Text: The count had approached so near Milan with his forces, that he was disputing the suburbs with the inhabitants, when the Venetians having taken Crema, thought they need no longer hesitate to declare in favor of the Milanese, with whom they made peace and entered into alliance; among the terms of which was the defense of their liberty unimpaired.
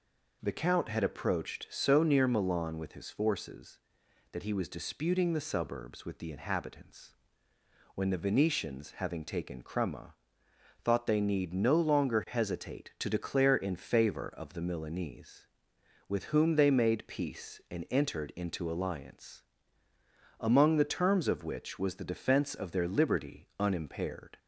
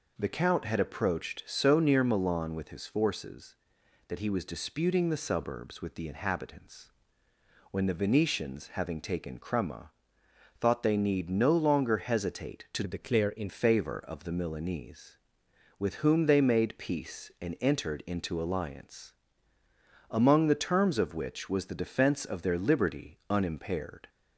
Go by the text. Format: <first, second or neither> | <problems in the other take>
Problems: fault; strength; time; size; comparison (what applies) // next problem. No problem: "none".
first | changes voice from "declare" to "in"; from 12.8 to 13.4 s; 0.6 s long